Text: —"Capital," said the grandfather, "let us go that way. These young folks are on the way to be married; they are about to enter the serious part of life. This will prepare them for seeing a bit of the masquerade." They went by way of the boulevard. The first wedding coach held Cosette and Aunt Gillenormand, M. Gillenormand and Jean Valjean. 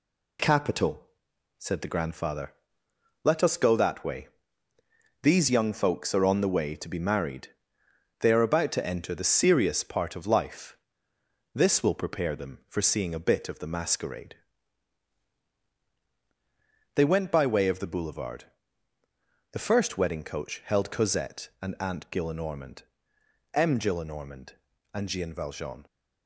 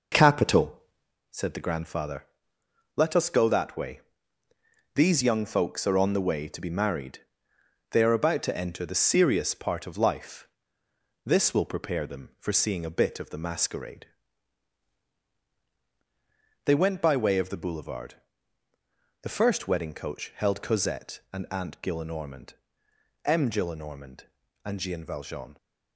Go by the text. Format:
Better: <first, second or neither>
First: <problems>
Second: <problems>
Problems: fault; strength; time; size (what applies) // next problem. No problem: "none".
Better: first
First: none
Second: starts louder than the rest; noticeable; until 1.2 s; 5 dB